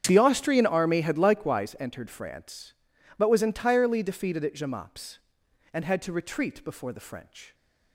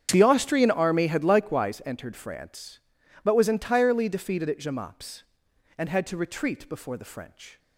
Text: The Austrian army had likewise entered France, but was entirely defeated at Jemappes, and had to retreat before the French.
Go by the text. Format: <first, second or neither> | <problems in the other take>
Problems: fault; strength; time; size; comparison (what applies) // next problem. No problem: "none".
neither | starts louder than the rest; strong; the same in both